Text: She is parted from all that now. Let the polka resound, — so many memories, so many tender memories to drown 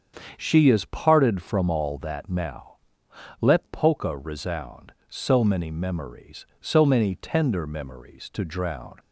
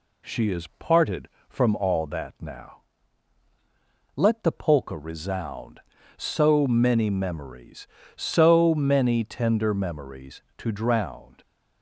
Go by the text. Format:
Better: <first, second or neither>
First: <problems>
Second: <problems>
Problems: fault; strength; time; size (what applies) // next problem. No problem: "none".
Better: second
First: starts louder than the rest; strong; until 1.3 s; 7.5 dB // skips "the"; at 3.6 s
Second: none